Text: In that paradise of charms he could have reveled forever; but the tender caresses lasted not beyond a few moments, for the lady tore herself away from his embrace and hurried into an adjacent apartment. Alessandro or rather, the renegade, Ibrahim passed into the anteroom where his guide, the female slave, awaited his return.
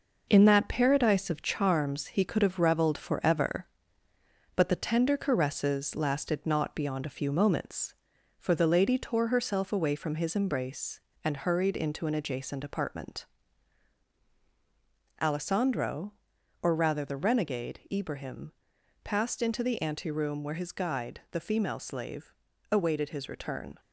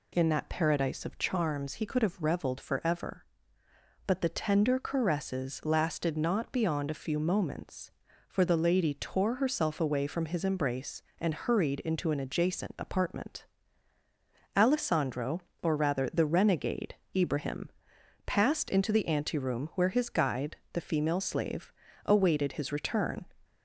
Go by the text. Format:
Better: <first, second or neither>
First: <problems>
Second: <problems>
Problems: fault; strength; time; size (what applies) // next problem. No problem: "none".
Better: second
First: gets quieter; noticeable; throughout; 5.5 dB // pauses between "Ibrahim" and "passed"; noticeable; at 18.5 s; 0.50 s long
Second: pauses between "Ibrahim" and "passed"; noticeable; at 17.7 s; 0.56 s long